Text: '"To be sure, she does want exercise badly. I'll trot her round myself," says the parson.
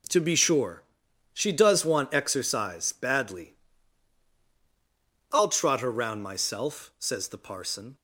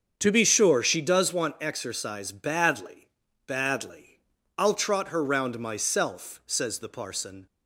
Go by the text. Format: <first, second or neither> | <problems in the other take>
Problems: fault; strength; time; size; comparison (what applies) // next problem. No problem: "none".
first | starts louder than the rest; until 1.1 s; 7 dB // says "badly" twice; at 3.4 s